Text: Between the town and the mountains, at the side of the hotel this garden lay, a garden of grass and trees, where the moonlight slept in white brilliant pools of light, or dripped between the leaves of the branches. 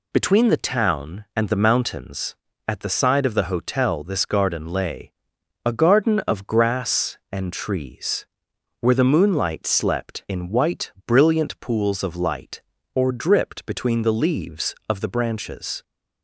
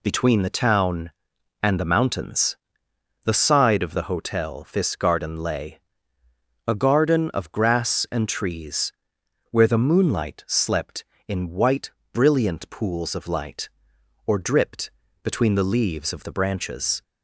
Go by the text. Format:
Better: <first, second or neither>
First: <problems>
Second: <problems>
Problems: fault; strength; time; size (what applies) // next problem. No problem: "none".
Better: first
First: none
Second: skips "at"; at 2.9 s // pauses between "white" and "brilliant"; slight; at 11.9 s; 0.22 s long // pauses between "dripped" and "between"; slight; at 14.9 s; 0.34 s long